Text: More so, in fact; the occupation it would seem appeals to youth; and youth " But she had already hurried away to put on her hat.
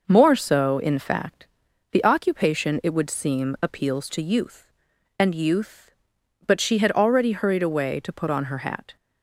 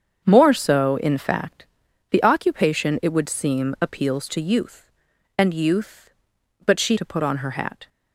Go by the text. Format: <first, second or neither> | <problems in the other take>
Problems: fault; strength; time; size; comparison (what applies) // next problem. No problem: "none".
first | starts louder than the rest; strong; until 1.3 s; 7.5 dB // skips "had already hurried away"; at 6.9 s